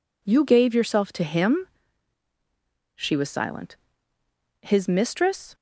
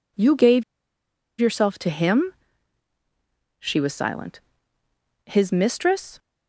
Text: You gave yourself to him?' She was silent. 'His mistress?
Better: first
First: none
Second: pauses between "gave" and "yourself"; noticeable; at 0.6 s; 0.76 s long

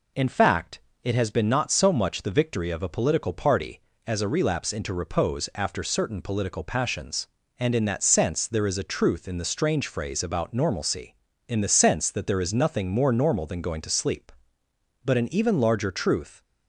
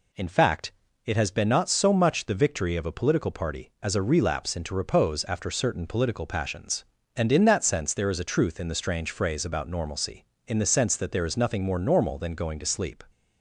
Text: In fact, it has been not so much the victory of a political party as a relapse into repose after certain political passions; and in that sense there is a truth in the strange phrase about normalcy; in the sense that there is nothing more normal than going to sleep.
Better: second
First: goes on to say "But an even larger truth"; from 15.0 s on; 1.3 s long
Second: none

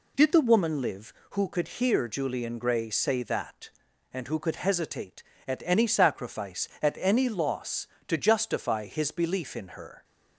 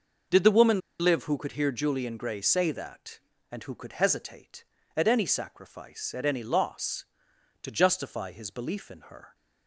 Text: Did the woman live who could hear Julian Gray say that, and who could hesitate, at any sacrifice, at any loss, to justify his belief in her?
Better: first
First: none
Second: pauses between "woman" and "live"; slight; at 0.7 s; 0.20 s long

